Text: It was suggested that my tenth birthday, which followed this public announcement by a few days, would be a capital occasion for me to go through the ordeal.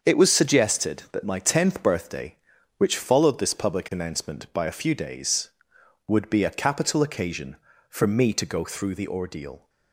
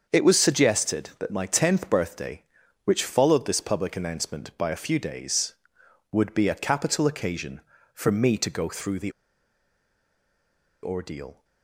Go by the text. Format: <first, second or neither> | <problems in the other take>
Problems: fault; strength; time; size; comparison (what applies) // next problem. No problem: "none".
first | starts louder than the rest; until 1.1 s; 6.5 dB; also in the first // pauses between "the" and "ordeal"; strong; at 9.1 s; 1.7 s long